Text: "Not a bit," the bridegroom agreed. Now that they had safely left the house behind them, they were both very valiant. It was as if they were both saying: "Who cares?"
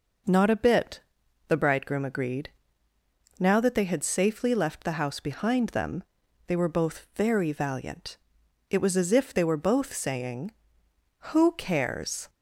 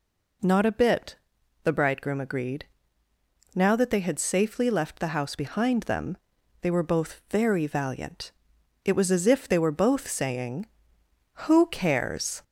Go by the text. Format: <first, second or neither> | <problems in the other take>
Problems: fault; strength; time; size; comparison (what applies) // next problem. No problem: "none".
first | gets louder; slight; throughout; 2 dB